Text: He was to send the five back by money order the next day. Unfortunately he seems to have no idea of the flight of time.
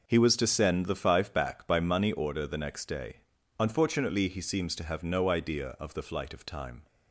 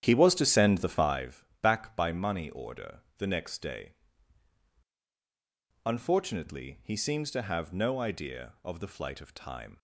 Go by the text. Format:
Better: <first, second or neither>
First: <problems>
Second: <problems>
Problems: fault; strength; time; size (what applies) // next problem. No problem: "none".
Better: first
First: none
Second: starts louder than the rest; strong; until 1.2 s; 10 dB // pauses between "five" and "back"; slight; at 1.4 s; 0.16 s long // pauses between "order" and "the"; slight; at 2.9 s; 0.18 s long